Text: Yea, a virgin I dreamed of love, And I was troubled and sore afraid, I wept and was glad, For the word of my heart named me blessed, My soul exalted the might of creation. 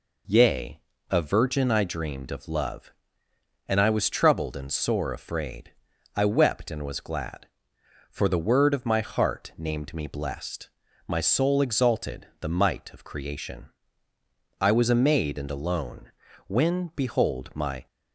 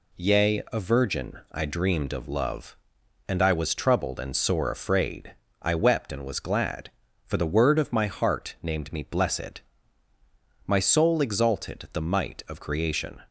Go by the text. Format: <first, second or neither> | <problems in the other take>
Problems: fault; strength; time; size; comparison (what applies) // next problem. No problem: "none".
second | goes on to say "I was a maid and alone When behold my"; strong; from 14.5 s on; 3.2 s long